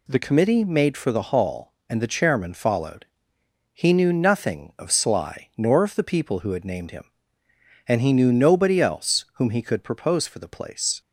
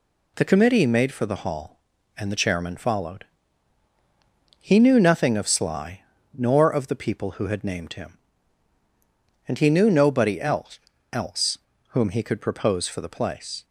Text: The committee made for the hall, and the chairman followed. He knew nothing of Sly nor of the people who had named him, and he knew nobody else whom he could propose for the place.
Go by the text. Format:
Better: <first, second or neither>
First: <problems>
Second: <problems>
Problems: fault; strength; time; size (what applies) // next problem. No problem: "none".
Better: first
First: none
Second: pauses between "Sly" and "nor"; slight; at 6.0 s; 0.32 s long // says "else" twice; at 11.1 s